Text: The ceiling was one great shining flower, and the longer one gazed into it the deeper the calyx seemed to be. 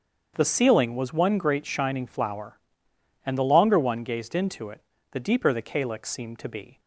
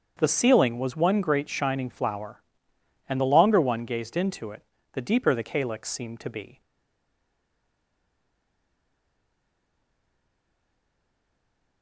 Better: first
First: starts louder than the rest; strong; until 1.3 s; 7 dB // pauses between "it" and "the"; slight; at 4.8 s; 0.32 s long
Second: starts louder than the rest; strong; until 1.1 s; 7 dB // pauses between "it" and "the"; slight; at 4.6 s; 0.32 s long // stays silent after the last word; strong; from 6.6 s on; 5.2 s long

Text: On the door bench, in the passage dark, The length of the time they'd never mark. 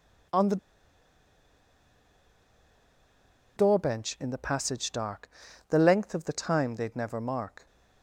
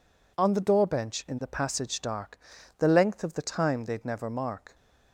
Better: second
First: pauses between "the" and "door"; strong; at 0.5 s; 3.0 s long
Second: none

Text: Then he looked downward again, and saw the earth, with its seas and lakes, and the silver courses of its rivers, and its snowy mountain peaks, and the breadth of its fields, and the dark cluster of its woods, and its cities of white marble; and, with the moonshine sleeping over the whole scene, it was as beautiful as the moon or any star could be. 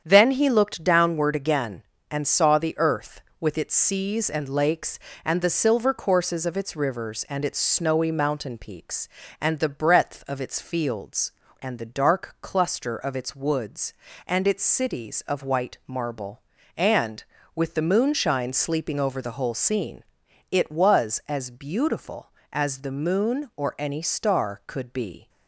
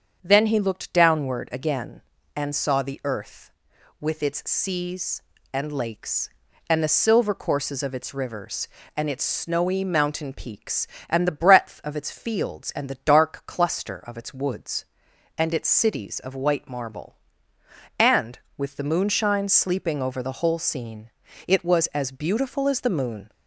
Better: first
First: starts louder than the rest; strong; until 1.0 s; 8 dB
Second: starts louder than the rest; until 1.2 s; 7 dB // stops before "or any star could be"; at 23.2 s

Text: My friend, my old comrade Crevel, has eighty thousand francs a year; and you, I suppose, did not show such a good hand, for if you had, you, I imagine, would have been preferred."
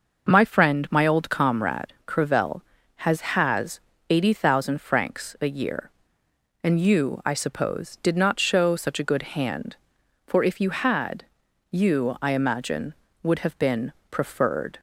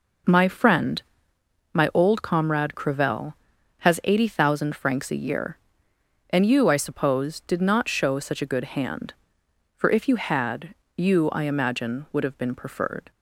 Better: second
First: says "has" twice; at 3.2 s // pauses between "been" and "preferred"; slight; at 13.9 s; 0.16 s long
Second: none

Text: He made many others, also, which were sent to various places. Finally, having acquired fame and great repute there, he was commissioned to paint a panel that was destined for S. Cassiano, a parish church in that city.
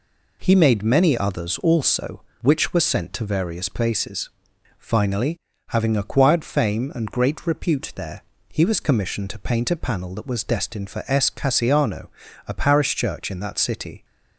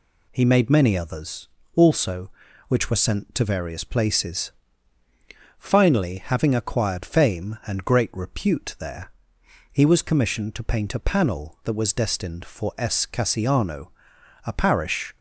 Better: first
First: none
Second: stops before "church in that city"; at 15.1 s

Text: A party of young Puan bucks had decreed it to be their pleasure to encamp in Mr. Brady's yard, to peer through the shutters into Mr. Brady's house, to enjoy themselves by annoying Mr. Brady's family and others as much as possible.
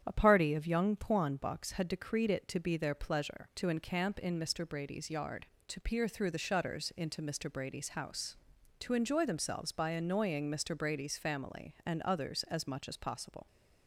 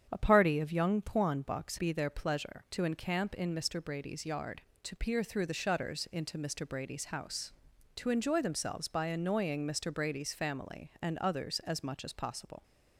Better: first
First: starts louder than the rest; strong; until 1.0 s; 9 dB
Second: starts louder than the rest; strong; until 1.1 s; 8.5 dB // skips "had decreed it to"; at 1.7 s

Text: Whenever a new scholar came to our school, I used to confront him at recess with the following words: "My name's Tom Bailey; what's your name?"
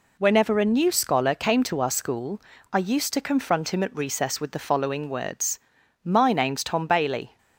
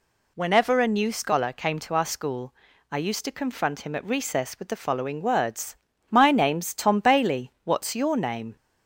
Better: second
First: stops before "what's your name"; at 7.3 s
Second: none

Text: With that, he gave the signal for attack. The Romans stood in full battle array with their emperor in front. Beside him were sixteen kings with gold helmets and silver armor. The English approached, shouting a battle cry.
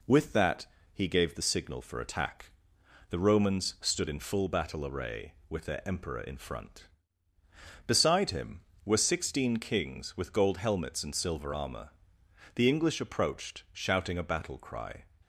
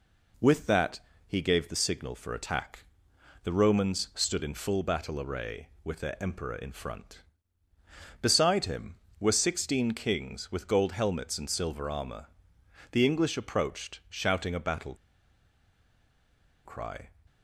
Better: first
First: none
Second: pauses between "battle" and "cry"; strong; at 14.9 s; 1.7 s long

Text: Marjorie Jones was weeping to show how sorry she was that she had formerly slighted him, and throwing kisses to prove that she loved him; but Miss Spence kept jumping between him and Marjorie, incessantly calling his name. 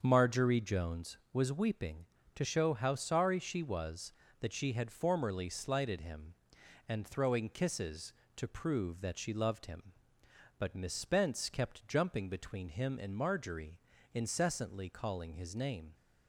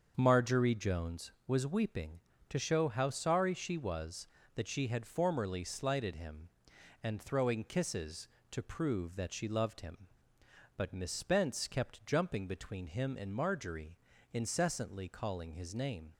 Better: neither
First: starts louder than the rest; until 1.0 s; 6.5 dB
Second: starts louder than the rest; until 1.1 s; 6.5 dB

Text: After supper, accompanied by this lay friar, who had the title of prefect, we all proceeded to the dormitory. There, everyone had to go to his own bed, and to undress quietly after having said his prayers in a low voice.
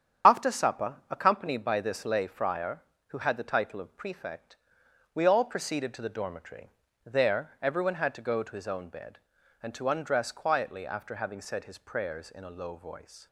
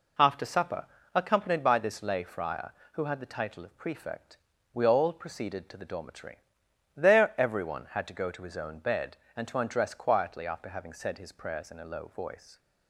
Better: second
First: loses the start of "After"; at 0.2 s; 55 ms // starts louder than the rest; strong; until 1.4 s; 8.5 dB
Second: none

